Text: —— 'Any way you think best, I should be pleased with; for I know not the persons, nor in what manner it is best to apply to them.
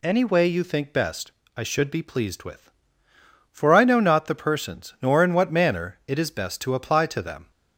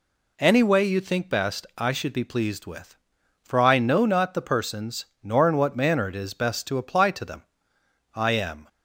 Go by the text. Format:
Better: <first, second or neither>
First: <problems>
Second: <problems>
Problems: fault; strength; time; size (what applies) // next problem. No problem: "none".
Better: first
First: none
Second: goes on to say "I am"; from 8.1 s on; 0.54 s long